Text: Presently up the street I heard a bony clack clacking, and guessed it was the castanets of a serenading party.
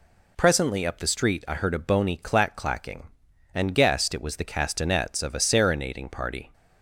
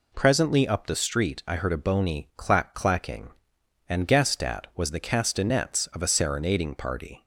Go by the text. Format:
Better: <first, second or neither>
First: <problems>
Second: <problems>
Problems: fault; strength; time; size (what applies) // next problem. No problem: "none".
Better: first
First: none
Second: says "at" for "it"; at 4.4 s